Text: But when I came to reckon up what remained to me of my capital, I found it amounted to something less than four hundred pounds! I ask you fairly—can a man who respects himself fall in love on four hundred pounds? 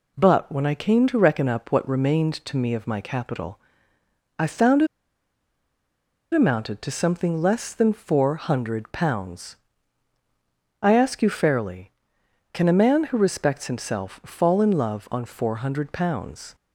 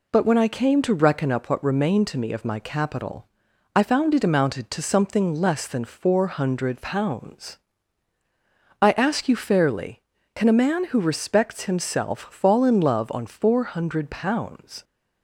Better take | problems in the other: second | pauses between "it" and "amounted"; strong; at 4.8 s; 1.4 s long

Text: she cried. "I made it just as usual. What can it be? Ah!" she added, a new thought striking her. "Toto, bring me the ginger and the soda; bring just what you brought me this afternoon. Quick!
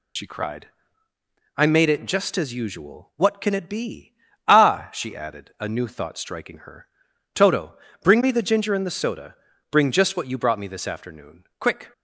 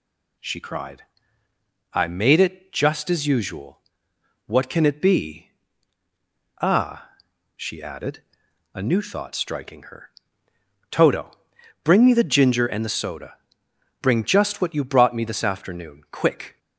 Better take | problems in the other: second | loses the start of "she"; at 0.1 s; 60 ms

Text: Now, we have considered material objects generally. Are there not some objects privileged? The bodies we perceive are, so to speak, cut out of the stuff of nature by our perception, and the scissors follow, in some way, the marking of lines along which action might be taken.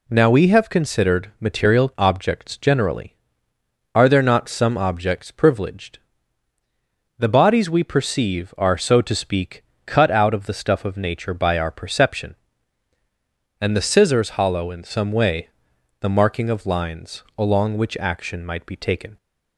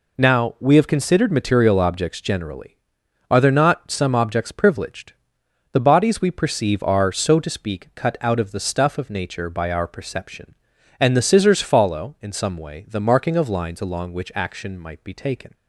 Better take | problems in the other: second | says "hollow" for "follow"; at 14.3 s

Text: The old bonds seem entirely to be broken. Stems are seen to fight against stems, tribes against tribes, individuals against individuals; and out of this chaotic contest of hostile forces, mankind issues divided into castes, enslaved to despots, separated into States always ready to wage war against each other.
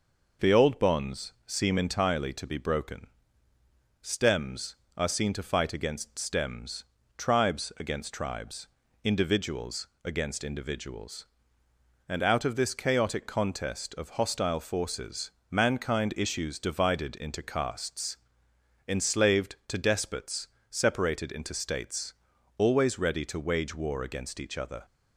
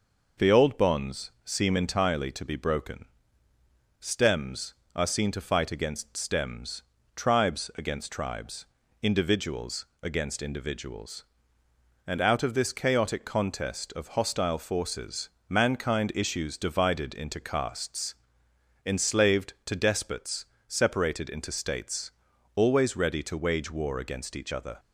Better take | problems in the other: neither | pauses between "individuals" and "against"; slight; the same in both // pauses between "States" and "always"; the same in both

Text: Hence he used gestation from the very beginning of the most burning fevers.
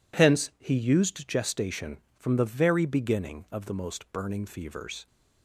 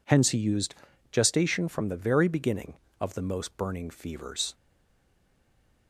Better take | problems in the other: first | pauses between "used" and "gestation"; slight; at 0.7 s; 0.36 s long // stays silent after the last word; noticeable; from 4.5 s on; 1.3 s long

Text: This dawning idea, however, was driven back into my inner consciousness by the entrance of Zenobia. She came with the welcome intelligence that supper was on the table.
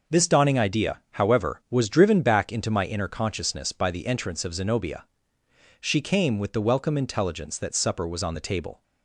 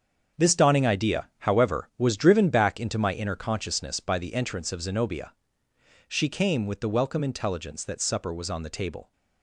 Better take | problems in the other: first | gets quieter; strong; throughout; 9 dB

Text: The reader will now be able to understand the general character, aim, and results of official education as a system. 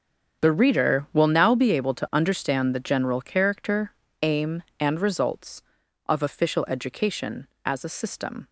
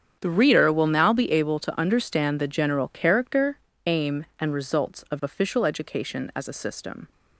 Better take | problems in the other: first | gets quieter; strong; throughout; 16 dB // starts louder than the rest; strong; until 1.2 s; 8.5 dB; strong in the first

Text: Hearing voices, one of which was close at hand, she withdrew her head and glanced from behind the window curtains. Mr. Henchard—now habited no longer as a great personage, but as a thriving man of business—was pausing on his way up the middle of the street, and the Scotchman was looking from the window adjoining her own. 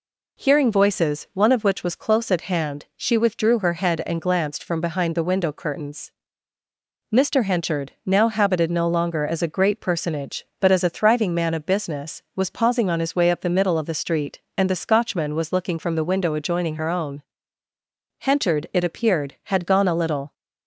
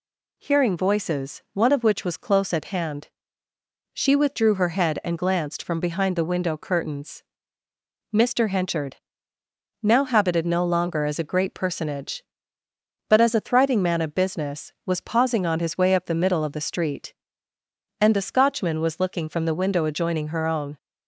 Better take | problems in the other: second | goes on to say "Henchard it appeared had gone a little"; strong; from 18.1 s on; 2.1 s long

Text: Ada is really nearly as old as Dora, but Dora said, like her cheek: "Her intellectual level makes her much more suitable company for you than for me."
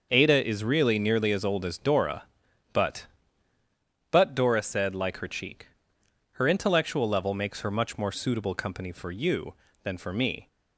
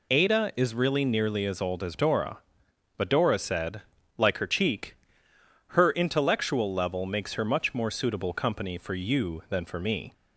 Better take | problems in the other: second | starts louder than the rest; until 1.1 s; 6.5 dB // says "but" twice; at 4.1 s

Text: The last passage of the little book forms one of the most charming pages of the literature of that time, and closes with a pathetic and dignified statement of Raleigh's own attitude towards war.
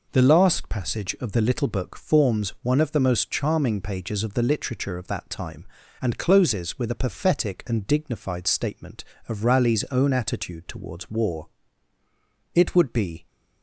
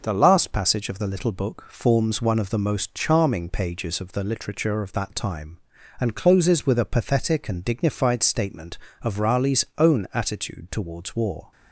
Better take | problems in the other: second | goes on to say "It would be"; noticeable; from 12.5 s on; 0.72 s long

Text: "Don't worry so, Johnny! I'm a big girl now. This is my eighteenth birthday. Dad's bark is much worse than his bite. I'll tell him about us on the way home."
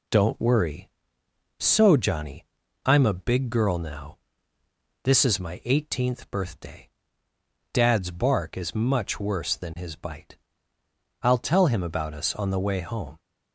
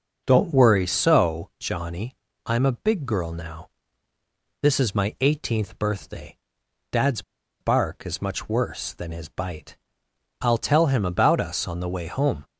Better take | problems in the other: first | starts louder than the rest; until 1.2 s; 6.5 dB // pauses between "Dad's" and "bark"; at 7.2 s; 0.39 s long

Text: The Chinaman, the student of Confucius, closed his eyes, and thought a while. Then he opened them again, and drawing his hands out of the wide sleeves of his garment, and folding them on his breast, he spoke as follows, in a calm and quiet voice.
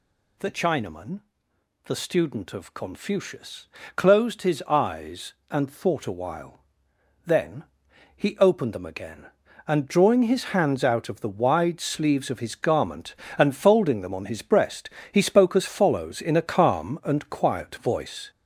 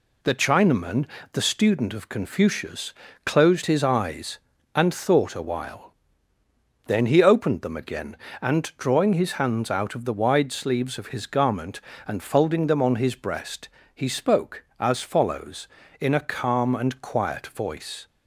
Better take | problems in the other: second | gets louder; noticeable; throughout; 5 dB // pauses between "Then" and "he"; noticeable; at 7.6 s; 0.50 s long

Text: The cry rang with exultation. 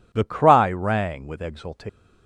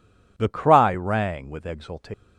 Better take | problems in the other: neither | none

